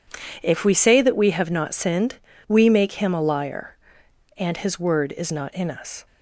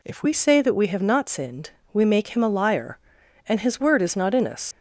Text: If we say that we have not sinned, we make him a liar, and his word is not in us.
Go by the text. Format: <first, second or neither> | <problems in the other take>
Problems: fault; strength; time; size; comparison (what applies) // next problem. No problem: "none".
first | leaves "us" unfinished; at 4.7 s; 80 ms